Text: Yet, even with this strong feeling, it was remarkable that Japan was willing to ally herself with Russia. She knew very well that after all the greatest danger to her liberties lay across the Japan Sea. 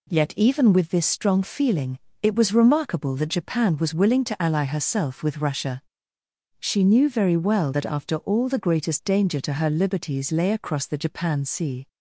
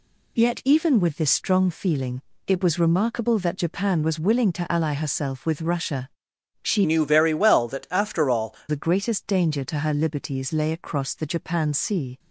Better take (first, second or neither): first